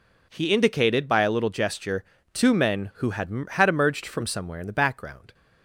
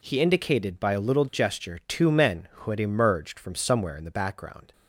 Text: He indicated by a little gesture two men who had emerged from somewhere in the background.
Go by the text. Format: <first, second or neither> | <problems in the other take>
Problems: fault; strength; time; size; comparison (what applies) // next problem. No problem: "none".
second | pauses between "gesture" and "two"; slight; at 2.0 s; 0.30 s long // says "had" twice; at 3.5 s